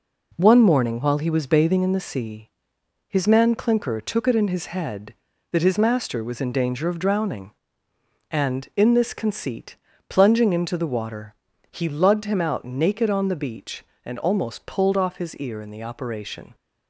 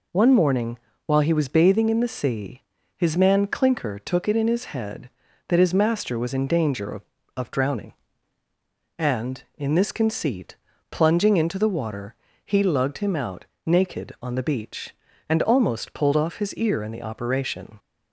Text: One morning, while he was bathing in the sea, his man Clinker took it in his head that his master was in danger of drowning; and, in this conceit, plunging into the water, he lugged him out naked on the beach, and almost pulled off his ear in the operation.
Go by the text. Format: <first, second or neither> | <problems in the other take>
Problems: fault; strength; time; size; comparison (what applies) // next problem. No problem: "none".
first | says "of" twice; at 7.3 s // pauses between "out" and "naked"; slight; at 13.4 s; 0.20 s long